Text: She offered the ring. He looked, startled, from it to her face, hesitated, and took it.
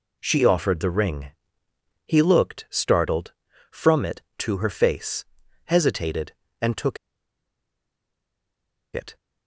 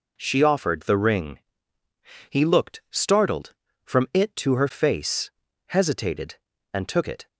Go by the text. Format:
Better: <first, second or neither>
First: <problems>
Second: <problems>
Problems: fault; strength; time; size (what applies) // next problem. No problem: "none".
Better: second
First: pauses between "took" and "it"; strong; at 6.9 s; 1.9 s long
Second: none